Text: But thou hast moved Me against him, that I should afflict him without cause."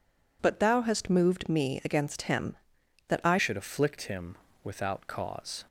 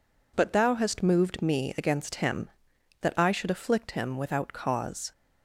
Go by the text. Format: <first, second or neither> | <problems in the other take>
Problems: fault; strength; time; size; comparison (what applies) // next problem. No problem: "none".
second | changes voice at "should"; from 3.3 s on; 2.3 s long // pauses between "him" and "without"; slight; at 4.3 s; 0.30 s long